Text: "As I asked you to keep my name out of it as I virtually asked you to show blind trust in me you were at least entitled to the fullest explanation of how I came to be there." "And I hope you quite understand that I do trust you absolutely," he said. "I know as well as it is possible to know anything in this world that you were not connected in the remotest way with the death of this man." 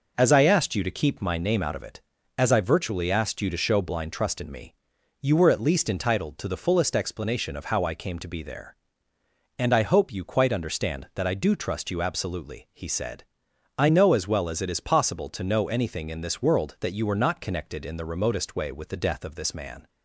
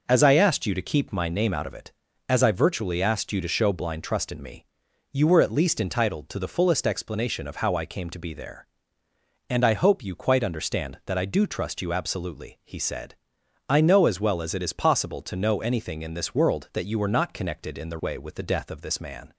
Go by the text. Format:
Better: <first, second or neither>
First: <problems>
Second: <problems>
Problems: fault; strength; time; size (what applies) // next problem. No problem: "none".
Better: first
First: pauses between "me" and "you"; noticeable; at 4.7 s; 0.48 s long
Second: pauses between "me" and "you"; noticeable; at 4.6 s; 0.48 s long // skips "remotest"; at 17.9 s